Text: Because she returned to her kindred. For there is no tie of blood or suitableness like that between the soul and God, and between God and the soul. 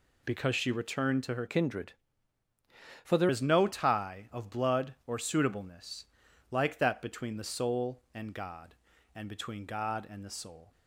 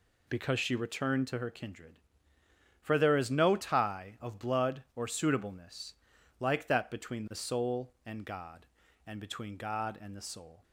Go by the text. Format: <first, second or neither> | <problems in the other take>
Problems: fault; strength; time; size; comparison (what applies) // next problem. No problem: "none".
second | changes voice from "kindred" to "there"; from 1.4 to 3.2 s; 1.8 s long // pauses between "suitableness" and "like"; noticeable; at 6.0 s; 0.46 s long; noticeable in the second